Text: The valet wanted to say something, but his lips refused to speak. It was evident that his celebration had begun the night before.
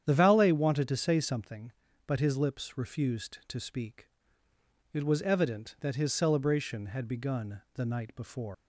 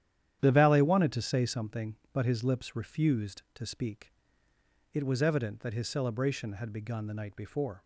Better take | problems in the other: second | starts louder than the rest; strong; until 1.0 s; 9 dB; strong in the second // leaves "before" unfinished; at 8.5 s; 155 ms

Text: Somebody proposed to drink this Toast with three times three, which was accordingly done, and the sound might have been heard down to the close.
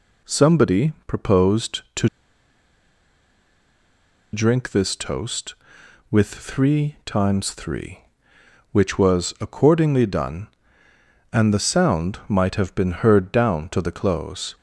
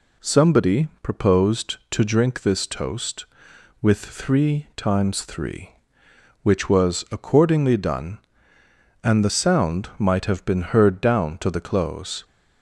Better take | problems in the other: second | pauses between "to" and "drink"; strong; at 2.0 s; 2.2 s long

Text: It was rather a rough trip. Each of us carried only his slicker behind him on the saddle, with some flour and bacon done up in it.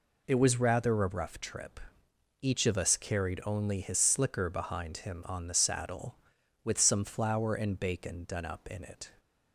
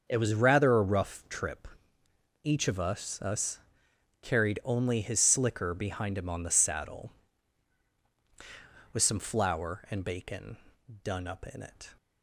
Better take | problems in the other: first | starts louder than the rest; until 1.0 s; 6.5 dB // says "us" twice; at 3.2 s // pauses between "bacon" and "done"; at 10.5 s; 0.44 s long

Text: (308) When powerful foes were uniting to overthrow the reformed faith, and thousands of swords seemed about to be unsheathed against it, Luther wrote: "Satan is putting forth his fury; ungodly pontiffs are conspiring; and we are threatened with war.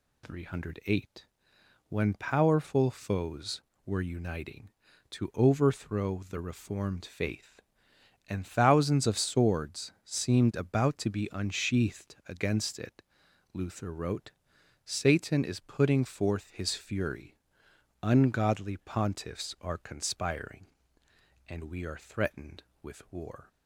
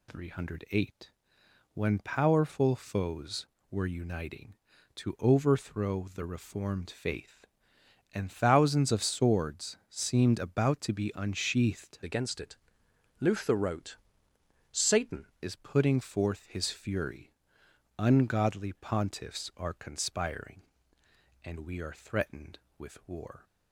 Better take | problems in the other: first | changes voice from "against" to "Satan"; from 12.0 to 15.2 s; 3.2 s long

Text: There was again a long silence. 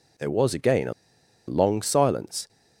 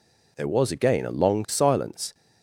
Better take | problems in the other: second | pauses between "a" and "long"; noticeable; at 0.9 s; 0.55 s long

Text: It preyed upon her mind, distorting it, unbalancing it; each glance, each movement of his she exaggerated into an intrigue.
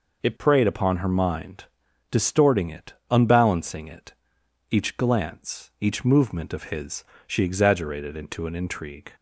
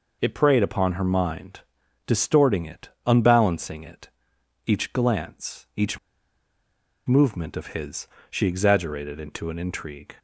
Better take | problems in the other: first | pauses between "each" and "movement"; at 5.9 s; 1.0 s long // pauses between "his" and "she"; slight; at 8.0 s; 0.22 s long; slight in the first

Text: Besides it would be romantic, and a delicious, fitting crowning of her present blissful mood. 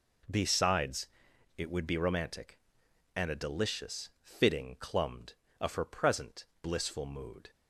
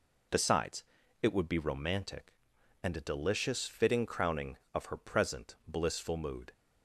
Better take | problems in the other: second | pauses between "Besides" and "it"; noticeable; at 1.0 s; 0.52 s long; also in the second // says "clumbed" for "crowning"; at 4.8 s // pauses between "present" and "blissful"; slight; at 6.4 s; 0.16 s long

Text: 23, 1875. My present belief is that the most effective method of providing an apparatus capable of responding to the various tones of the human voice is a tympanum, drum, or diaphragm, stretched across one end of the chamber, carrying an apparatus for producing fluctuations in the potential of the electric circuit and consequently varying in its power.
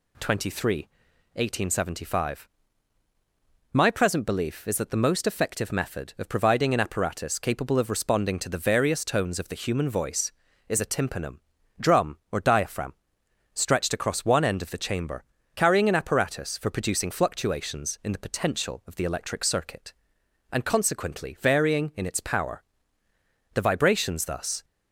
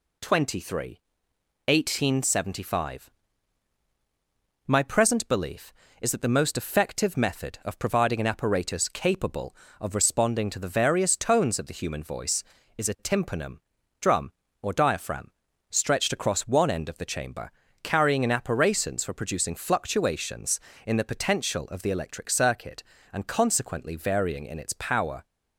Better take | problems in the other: second | goes on to say "The vibrations thus"; noticeable; from 23.5 s on; 1.1 s long

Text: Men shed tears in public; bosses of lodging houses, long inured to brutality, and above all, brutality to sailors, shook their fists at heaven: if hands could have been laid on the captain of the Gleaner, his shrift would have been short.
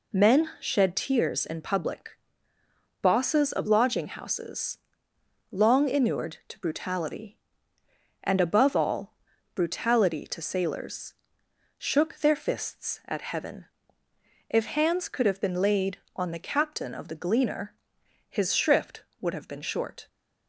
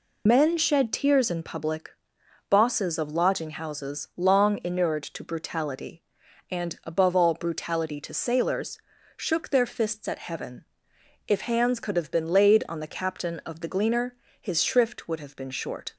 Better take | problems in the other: first | loses the start of "Men"; at 0.2 s; 70 ms

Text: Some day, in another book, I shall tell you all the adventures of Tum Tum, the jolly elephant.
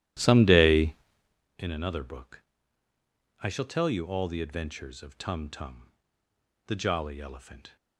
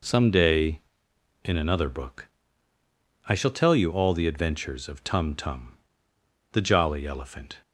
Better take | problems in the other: second | starts louder than the rest; strong; until 1.5 s; 13 dB

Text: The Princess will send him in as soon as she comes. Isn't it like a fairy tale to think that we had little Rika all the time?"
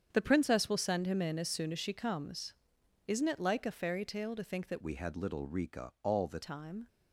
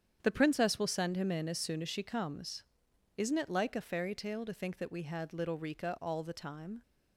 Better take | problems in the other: second | starts louder than the rest; strong; until 1.1 s; 8 dB; strong in the second // changes voice from "we" to "the"; from 4.8 to 6.4 s; 1.6 s long

